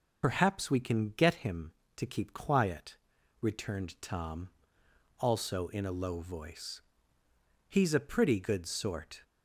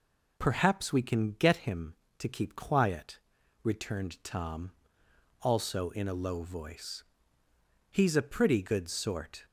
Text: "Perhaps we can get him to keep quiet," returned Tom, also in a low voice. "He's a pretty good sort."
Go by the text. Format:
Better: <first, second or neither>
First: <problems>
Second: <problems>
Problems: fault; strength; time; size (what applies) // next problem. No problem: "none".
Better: second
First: loses the start of "Perhaps"; at 0.2 s; 65 ms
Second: none